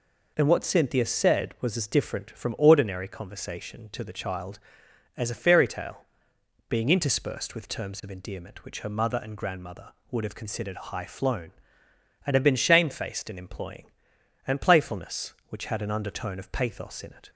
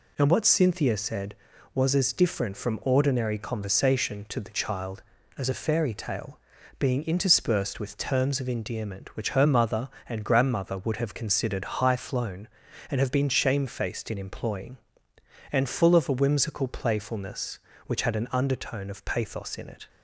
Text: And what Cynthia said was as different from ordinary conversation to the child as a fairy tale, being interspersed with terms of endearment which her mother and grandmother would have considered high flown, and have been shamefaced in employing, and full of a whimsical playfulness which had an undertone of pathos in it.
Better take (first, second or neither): second